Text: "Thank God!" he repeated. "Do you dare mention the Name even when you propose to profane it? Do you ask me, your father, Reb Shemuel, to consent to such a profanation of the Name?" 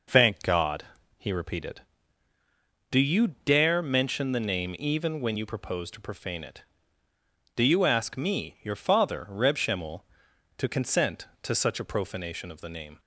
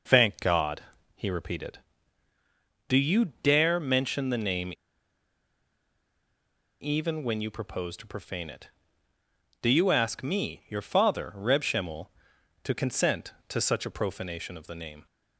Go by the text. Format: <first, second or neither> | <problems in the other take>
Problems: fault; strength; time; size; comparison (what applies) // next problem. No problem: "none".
first | pauses between "Name" and "even"; strong; at 4.7 s; 2.0 s long